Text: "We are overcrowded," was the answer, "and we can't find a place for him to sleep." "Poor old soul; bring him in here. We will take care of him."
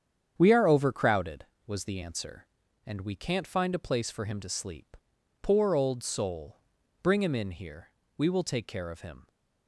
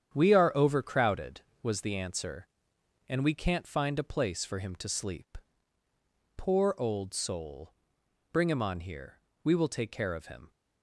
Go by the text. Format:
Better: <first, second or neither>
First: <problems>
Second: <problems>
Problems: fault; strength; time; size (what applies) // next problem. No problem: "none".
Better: first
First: starts louder than the rest; strong; until 1.3 s; 8 dB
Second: starts louder than the rest; strong; until 1.1 s; 9 dB // says "on" for "in"; at 8.6 s